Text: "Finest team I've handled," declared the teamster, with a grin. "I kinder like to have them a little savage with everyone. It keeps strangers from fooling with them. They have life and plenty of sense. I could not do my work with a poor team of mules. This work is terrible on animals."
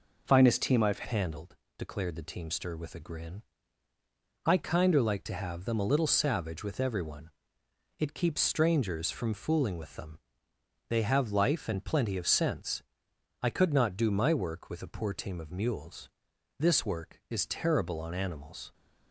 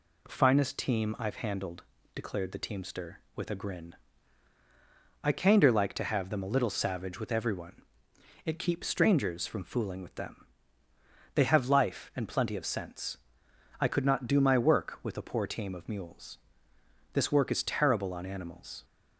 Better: second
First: changes voice at "handled"; from 1.0 s on; 17.7 s long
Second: none

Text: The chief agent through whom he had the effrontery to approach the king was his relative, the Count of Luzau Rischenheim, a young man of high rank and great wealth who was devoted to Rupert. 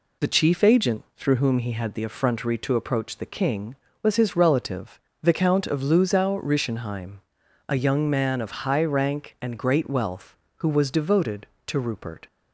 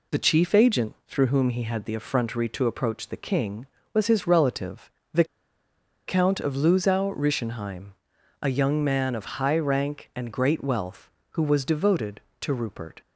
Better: first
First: none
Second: pauses between "the" and "Count"; noticeable; at 5.2 s; 0.83 s long

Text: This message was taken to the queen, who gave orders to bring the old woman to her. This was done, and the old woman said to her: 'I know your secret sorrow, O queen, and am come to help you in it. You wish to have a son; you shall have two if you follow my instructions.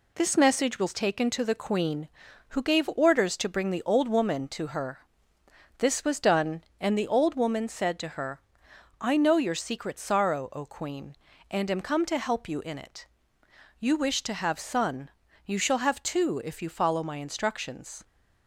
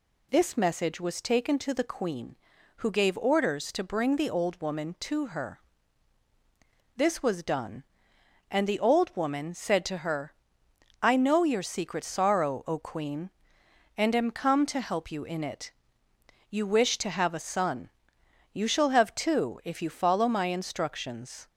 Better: second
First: skips "a"; at 14.5 s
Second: none

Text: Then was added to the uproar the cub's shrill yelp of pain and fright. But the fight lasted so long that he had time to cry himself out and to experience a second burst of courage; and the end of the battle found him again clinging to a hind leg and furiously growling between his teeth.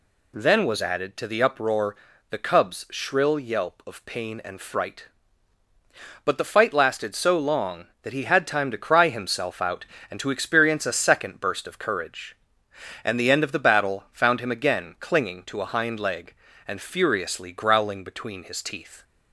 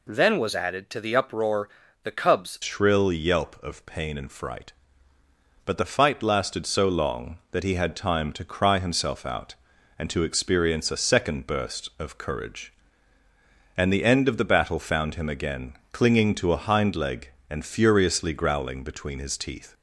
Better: first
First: pauses between "uproar" and "the"; slight; at 1.9 s; 0.36 s long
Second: pauses between "uproar" and "the"; slight; at 1.6 s; 0.36 s long // changes voice at "shrill"; from 2.6 s on; 17.1 s long // pauses between "again" and "clinging"; slight; at 15.7 s; 0.18 s long

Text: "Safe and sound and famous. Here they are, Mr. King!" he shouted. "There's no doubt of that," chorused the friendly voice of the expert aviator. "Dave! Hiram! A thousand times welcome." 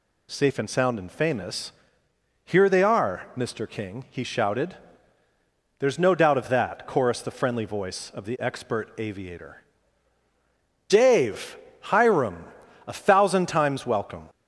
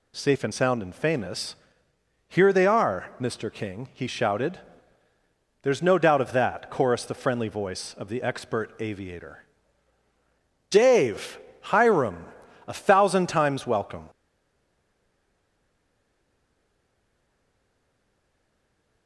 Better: first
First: none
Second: stays silent after the last word; strong; from 14.0 s on; 5.0 s long

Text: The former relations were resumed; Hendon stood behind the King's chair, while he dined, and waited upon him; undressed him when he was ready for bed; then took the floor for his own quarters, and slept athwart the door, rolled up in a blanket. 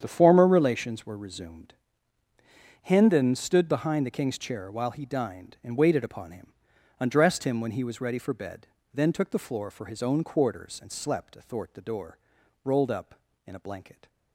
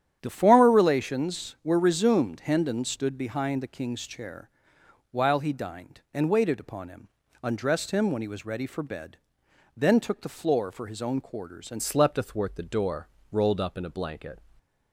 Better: first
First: starts louder than the rest; strong; until 1.0 s; 8.5 dB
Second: starts louder than the rest; strong; until 1.2 s; 9.5 dB // changes voice at "slept"; from 11.8 s on; 2.6 s long

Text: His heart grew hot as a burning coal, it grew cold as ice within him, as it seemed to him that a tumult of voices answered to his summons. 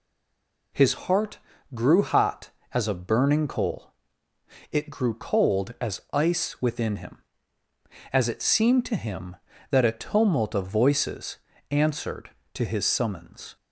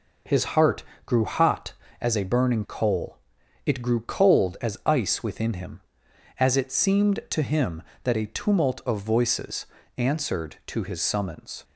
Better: second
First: stays silent before the first word; slight; until 0.7 s; 0.7 s long // pauses between "heart" and "grew"; slight; at 1.3 s; 0.36 s long // pauses between "voices" and "answered"; slight; at 11.3 s; 0.32 s long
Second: pauses between "heart" and "grew"; slight; at 0.8 s; 0.22 s long // pauses between "voices" and "answered"; slight; at 9.6 s; 0.32 s long

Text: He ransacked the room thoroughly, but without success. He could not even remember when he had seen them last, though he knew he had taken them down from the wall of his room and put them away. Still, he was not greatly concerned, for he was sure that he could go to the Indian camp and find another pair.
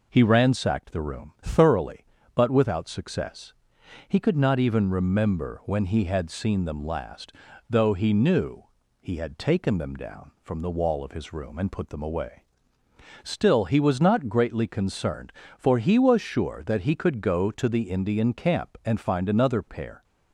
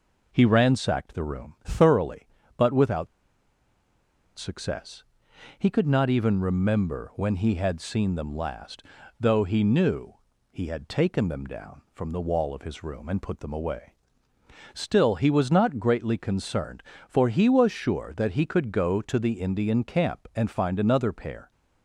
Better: first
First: pauses between "knew" and "he"; slight; at 8.6 s; 0.36 s long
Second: pauses between "without" and "success"; strong; at 3.0 s; 1.3 s long // pauses between "knew" and "he"; slight; at 10.1 s; 0.36 s long

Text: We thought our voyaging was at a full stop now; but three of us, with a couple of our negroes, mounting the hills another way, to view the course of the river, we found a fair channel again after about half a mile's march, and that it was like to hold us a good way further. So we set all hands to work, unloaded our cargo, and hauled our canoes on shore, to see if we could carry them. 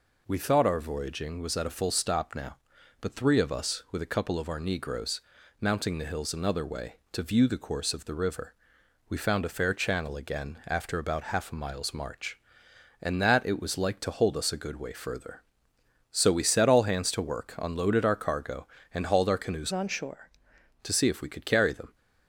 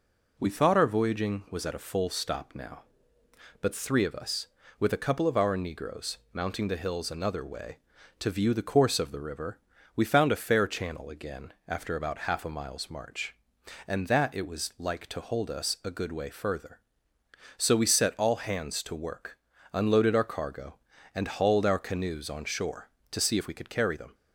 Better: second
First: changes voice from "on" to "shore"; from 19.7 to 20.2 s; 0.5 s long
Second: none

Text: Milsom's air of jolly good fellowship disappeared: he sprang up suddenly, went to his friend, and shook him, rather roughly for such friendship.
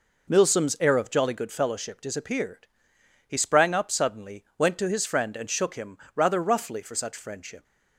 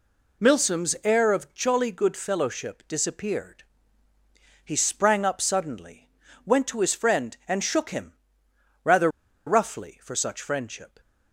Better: first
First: none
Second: pauses between "rather" and "roughly"; at 9.0 s; 0.38 s long

